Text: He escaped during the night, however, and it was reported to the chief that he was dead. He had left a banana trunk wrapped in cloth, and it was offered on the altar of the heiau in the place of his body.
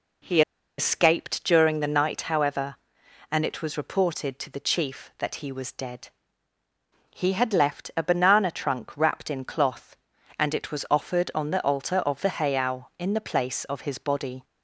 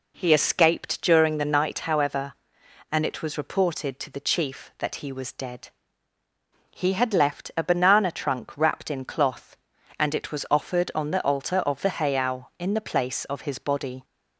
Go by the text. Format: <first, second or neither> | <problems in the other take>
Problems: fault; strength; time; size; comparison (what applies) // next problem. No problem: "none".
second | pauses between "He" and "escaped"; at 0.4 s; 0.37 s long